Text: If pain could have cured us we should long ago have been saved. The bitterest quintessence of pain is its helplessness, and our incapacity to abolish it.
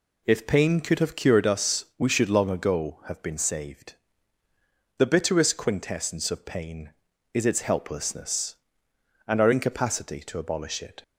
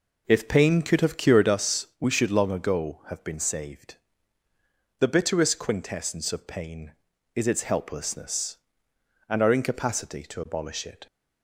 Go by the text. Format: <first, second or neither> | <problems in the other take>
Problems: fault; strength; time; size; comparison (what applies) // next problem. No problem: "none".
first | starts louder than the rest; noticeable; until 1.7 s; 4 dB